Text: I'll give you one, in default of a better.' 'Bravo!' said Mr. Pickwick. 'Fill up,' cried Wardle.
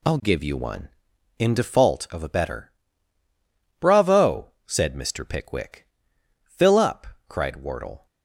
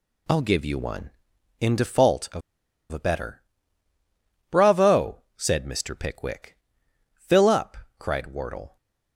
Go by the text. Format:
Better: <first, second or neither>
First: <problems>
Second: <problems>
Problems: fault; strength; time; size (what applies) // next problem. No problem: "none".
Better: first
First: none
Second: pauses between "of" and "a"; noticeable; at 2.4 s; 0.51 s long